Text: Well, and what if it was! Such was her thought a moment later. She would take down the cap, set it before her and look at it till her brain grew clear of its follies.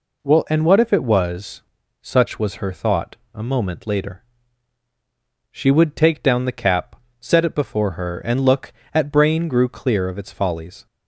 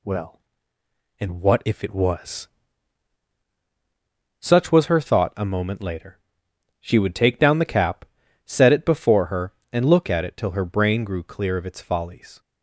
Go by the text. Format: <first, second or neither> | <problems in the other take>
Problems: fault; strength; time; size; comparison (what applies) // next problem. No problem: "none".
second | pauses between "thought" and "a"; slight; at 3.1 s; 0.18 s long // skips "it till her"; at 9.1 s